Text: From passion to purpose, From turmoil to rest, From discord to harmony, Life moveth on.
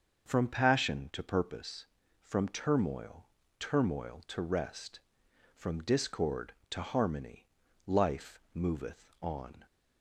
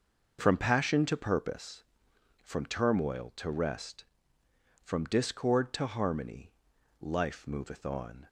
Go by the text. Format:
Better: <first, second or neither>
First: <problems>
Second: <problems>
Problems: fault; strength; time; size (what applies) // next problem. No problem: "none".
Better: second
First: starts louder than the rest; until 1.3 s; 6 dB // says "turmoil" twice; at 3.5 s // pauses between "Life" and "moveth"; slight; at 8.3 s; 0.16 s long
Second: none